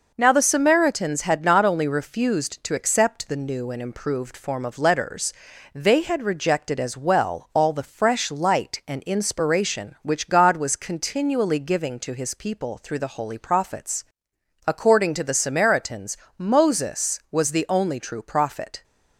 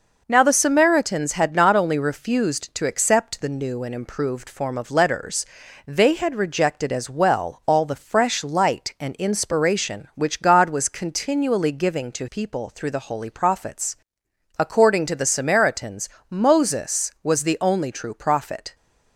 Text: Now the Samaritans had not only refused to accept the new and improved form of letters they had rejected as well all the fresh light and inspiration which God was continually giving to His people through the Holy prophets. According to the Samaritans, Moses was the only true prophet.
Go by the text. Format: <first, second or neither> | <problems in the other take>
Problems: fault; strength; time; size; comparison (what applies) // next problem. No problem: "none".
first | pauses between "letters" and "they"; at 5.4 s; 0.40 s long; also in the first // skips "His"; at 12.2 s